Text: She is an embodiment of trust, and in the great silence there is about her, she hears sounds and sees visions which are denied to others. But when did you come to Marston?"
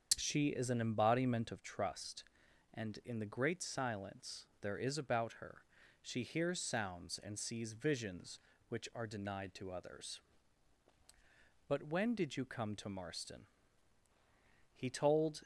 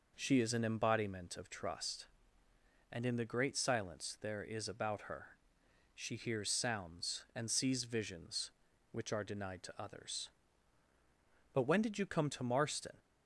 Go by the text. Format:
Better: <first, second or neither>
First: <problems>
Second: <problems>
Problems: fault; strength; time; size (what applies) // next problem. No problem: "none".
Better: second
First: starts louder than the rest; until 1.1 s; 7 dB // goes on to say "He told"; noticeable; from 14.7 s on; 0.68 s long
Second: none